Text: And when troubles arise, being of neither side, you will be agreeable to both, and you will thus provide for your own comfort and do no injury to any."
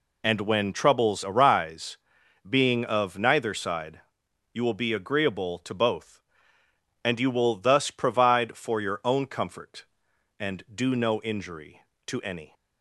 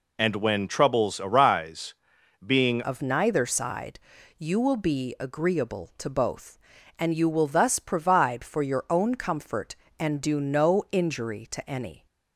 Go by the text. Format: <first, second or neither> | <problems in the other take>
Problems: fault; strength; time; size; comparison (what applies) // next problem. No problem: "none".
first | changes voice at "of"; from 2.8 s on; 9.2 s long